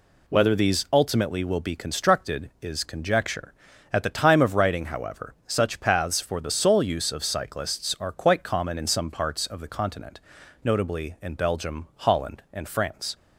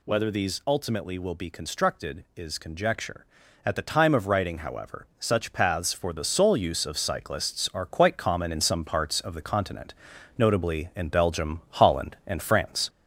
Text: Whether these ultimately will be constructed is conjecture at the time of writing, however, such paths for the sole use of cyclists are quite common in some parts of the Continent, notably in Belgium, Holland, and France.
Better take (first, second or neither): first